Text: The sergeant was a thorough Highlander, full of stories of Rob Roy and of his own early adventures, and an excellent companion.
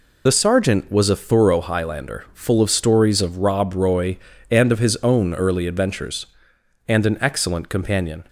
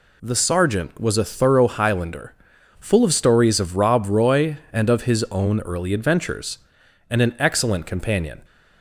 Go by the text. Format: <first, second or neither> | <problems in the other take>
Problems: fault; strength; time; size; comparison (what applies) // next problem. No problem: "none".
second | loses the start of "The"; at 0.2 s; 50 ms